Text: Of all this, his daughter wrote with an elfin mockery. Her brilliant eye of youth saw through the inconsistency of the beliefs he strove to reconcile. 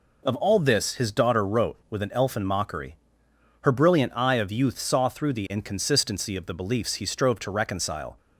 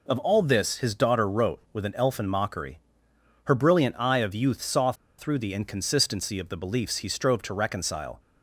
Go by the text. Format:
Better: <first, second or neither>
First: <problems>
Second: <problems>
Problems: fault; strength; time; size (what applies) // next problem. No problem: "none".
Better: first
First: none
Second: pauses between "saw" and "through"; slight; at 4.9 s; 0.25 s long